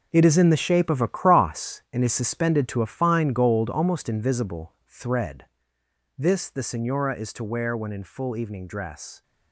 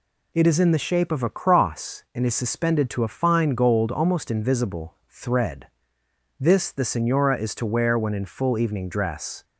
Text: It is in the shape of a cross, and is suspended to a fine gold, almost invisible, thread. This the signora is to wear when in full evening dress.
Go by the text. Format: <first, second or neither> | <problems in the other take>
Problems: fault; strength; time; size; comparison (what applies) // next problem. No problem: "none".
second | gets quieter; strong; throughout; 11.5 dB